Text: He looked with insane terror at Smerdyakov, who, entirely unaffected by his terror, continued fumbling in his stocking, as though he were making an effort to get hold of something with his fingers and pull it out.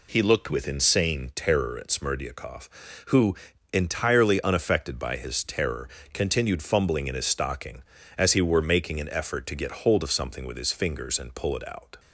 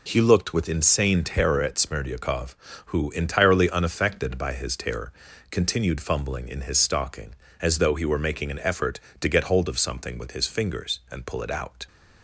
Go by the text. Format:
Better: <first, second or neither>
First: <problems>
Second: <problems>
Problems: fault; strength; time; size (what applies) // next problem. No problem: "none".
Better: second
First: skips "though"; at 8.3 s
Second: none